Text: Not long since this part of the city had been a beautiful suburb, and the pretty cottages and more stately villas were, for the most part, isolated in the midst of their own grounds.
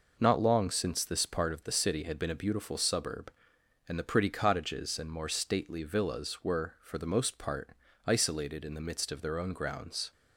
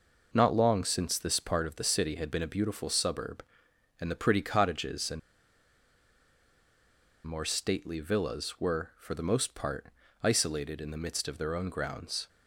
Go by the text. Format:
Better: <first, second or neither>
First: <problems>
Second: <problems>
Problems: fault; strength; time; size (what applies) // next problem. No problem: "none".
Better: first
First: none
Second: pauses between "and" and "more"; strong; at 5.1 s; 2.0 s long